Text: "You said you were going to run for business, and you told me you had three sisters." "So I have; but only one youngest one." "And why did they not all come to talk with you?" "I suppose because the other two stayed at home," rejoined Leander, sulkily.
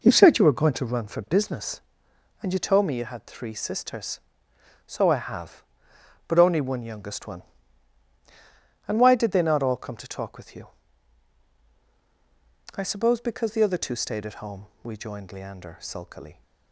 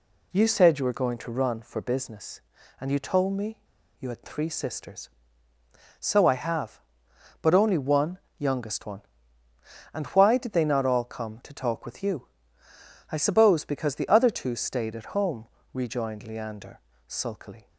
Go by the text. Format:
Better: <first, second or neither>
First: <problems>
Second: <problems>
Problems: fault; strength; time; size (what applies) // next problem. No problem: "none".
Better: first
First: none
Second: pauses between "me" and "you"; at 3.5 s; 0.41 s long // pauses between "one" and "youngest"; slight; at 8.1 s; 0.20 s long